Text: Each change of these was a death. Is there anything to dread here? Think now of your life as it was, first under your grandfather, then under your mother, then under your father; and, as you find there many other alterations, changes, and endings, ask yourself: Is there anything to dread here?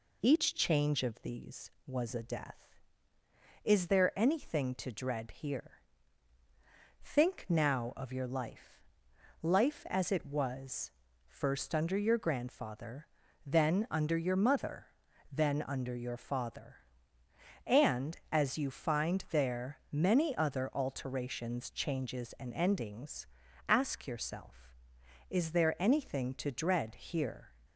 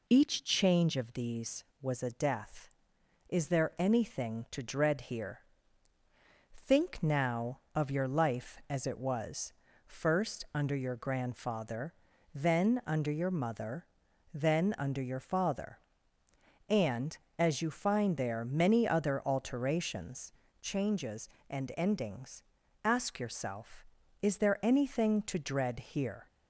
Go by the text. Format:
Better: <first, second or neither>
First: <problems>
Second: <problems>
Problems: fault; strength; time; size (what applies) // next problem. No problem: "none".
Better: second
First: says "life" twice; at 9.4 s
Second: none